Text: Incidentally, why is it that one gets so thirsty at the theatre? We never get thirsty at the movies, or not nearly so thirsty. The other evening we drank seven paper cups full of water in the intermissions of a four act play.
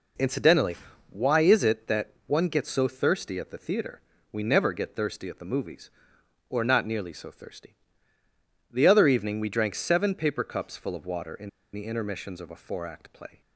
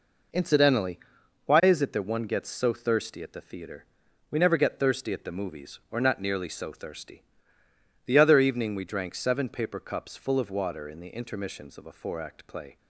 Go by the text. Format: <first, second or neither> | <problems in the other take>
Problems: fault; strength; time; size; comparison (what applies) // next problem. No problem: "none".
second | pauses between "in" and "the"; slight; at 11.4 s; 0.24 s long